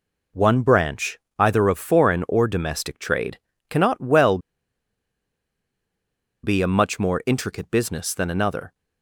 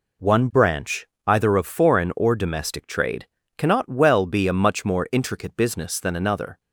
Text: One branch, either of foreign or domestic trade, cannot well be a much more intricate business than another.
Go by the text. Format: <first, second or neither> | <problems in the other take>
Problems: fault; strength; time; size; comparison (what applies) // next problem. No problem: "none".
second | pauses between "well" and "be"; strong; at 4.3 s; 2.0 s long